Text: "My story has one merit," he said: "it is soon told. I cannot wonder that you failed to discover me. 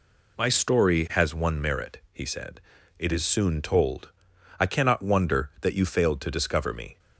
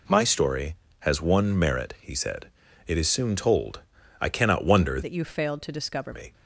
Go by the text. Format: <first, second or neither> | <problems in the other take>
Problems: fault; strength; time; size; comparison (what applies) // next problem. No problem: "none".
first | changes voice from "that" to "discover"; from 5.0 to 6.1 s; 1.1 s long